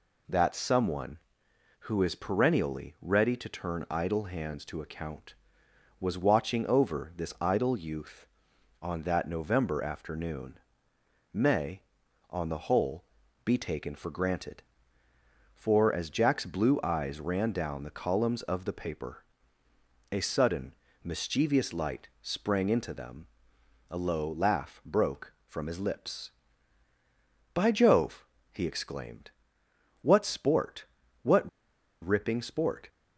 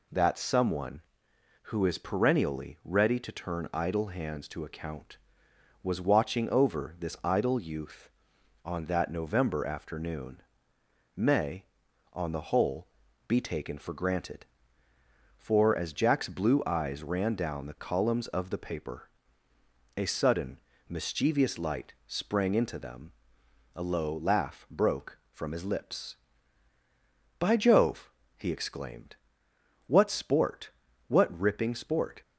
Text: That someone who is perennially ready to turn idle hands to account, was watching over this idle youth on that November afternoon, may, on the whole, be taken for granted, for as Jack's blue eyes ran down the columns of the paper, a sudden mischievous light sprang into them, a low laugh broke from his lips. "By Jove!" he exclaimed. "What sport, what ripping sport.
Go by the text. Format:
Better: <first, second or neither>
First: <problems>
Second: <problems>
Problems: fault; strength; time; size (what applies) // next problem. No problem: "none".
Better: second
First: pauses between "sudden" and "mischievous"; slight; at 20.7 s; 0.30 s long // pauses between "what" and "ripping"; noticeable; at 31.4 s; 0.53 s long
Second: pauses between "sudden" and "mischievous"; slight; at 20.5 s; 0.30 s long